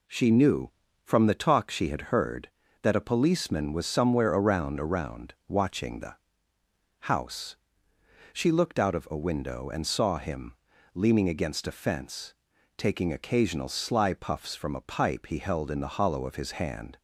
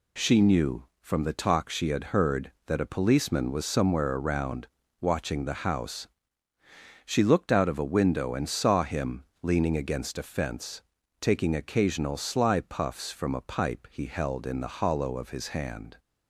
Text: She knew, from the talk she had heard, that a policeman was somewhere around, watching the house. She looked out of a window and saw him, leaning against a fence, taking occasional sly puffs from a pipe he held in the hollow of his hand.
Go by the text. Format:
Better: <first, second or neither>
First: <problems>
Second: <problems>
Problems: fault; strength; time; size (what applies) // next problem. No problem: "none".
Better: second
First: says "around" twice; at 4.7 s // pauses between "the" and "house"; noticeable; at 6.1 s; 0.84 s long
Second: none